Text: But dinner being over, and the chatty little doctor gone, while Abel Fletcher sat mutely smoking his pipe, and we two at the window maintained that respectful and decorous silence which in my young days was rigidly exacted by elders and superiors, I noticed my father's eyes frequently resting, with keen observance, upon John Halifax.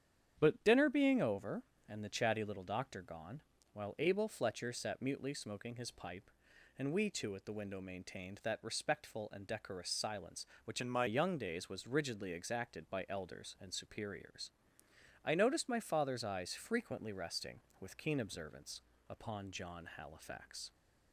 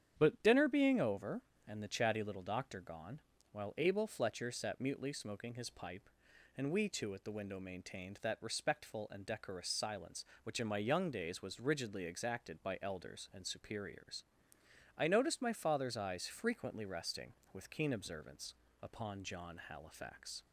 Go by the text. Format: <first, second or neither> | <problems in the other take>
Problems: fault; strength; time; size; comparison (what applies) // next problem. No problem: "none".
second | starts louder than the rest; strong; until 1.4 s; 9 dB; strong in the second // changes voice from "in" to "my"; from 10.8 to 11.0 s; 0.2 s long